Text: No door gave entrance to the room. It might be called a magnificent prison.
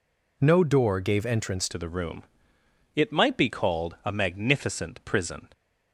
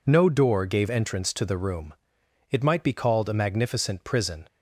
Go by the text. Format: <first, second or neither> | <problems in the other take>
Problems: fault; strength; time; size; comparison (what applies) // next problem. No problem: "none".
second | changes voice at "to"; from 1.6 s on; 3.8 s long